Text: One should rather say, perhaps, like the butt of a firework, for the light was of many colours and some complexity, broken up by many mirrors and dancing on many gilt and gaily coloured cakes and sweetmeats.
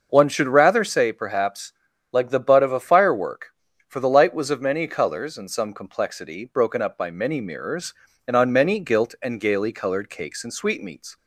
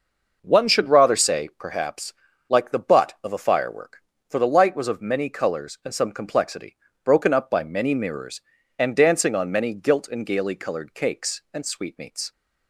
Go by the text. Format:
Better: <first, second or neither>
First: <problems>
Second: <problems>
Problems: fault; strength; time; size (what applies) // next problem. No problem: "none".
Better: second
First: starts louder than the rest; noticeable; until 1.1 s; 6 dB // skips "dancing"; at 8.3 s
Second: none